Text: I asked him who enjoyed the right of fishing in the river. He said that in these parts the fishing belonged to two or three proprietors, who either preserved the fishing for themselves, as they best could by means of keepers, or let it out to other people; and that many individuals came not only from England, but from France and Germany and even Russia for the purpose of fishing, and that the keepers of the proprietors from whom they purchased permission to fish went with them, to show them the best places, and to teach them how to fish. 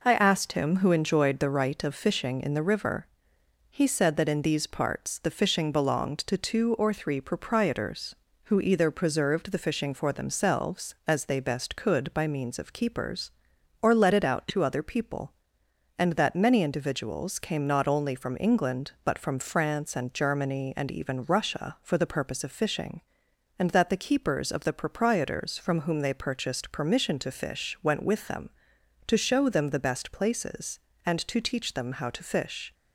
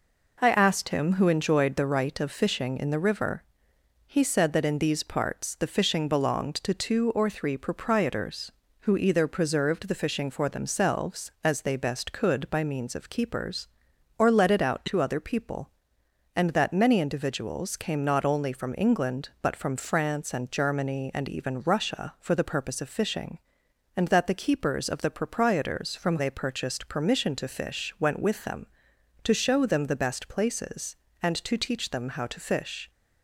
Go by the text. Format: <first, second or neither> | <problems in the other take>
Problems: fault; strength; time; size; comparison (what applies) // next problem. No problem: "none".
first | skips "whom"; at 26.1 s